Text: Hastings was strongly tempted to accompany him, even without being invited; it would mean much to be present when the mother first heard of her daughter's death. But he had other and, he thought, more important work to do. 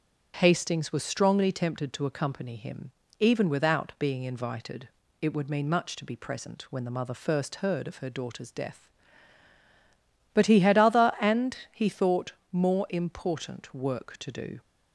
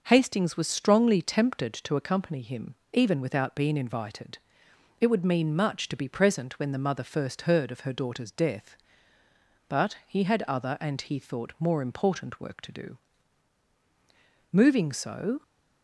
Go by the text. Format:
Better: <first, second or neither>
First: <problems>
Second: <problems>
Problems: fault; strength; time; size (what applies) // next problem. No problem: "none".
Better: first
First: none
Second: goes on to say "Moving so"; noticeable; from 14.5 s on; 0.92 s long